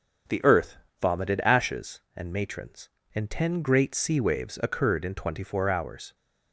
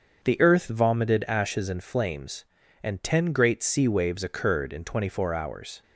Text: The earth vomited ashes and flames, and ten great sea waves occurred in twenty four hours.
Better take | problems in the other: second | starts louder than the rest; strong; until 1.6 s; 7.5 dB; also in the second // pauses between "earth" and "vomited"; slight; at 0.7 s; 0.26 s long // says "matrons" for "flames"; at 2.3 s

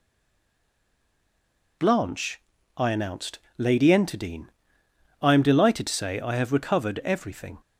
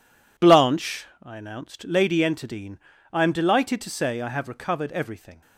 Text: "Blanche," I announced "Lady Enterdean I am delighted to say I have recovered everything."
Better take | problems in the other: second | stays silent before the first word; noticeable; until 1.7 s; 1.7 s long // pauses between "announced" and "Lady"; slight; at 3.3 s; 0.18 s long // pauses between "Enterdean" and "I"; noticeable; at 4.4 s; 0.76 s long; slight in the second

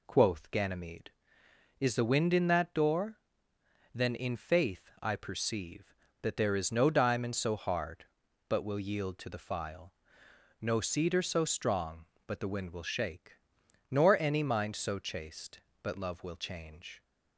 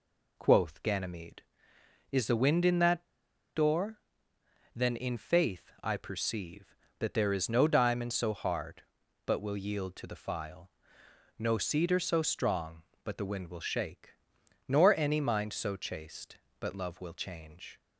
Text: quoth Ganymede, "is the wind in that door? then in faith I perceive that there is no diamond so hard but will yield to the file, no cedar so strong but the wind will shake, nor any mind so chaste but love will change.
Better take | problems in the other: first | pauses between "that" and "door"; noticeable; at 3.0 s; 0.49 s long

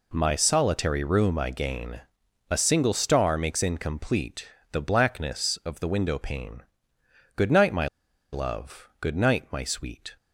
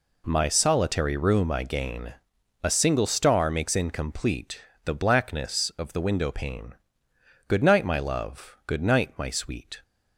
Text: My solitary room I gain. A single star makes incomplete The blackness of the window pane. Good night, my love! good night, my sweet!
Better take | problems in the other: second | pauses between "incomplete" and "The"; slight; at 4.4 s; 0.26 s long; slight in the second // pauses between "my" and "love"; noticeable; at 7.8 s; 0.46 s long

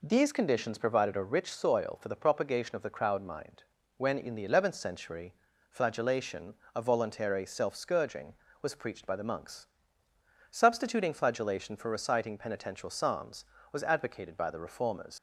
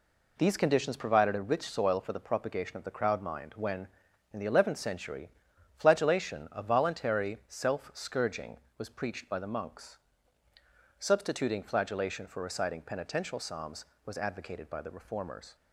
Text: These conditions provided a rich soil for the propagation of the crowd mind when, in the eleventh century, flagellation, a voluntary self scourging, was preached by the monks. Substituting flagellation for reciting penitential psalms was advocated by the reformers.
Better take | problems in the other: second | pauses between "mind" and "when"; slight; at 3.6 s; 0.32 s long // leaves "reformers" unfinished; at 15.1 s; 80 ms

